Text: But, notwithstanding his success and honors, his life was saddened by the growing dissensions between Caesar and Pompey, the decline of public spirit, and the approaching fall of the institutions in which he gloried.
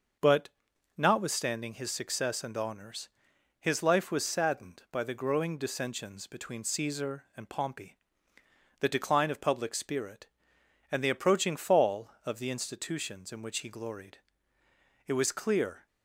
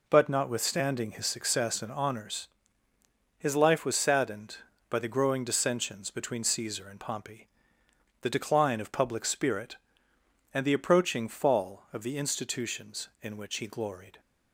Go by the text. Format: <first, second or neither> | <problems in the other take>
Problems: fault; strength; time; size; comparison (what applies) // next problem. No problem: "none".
second | starts louder than the rest; noticeable; until 1.6 s; 6 dB // goes on to say "It was clear"; noticeable; from 15.0 s on; 0.80 s long